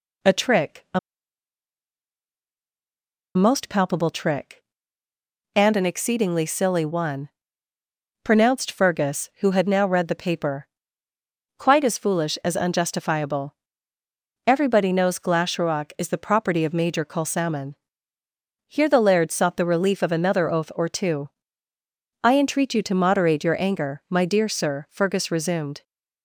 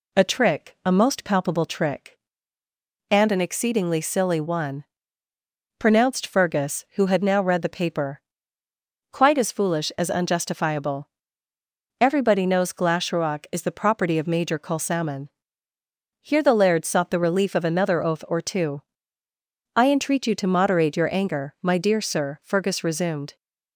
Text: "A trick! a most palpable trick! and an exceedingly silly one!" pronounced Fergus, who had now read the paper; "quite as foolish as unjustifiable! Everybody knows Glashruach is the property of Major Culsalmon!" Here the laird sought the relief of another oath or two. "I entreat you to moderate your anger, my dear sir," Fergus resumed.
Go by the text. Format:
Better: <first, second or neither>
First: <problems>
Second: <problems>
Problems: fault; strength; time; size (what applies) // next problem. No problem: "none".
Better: second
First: pauses between "a" and "most"; strong; at 0.9 s; 2.3 s long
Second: none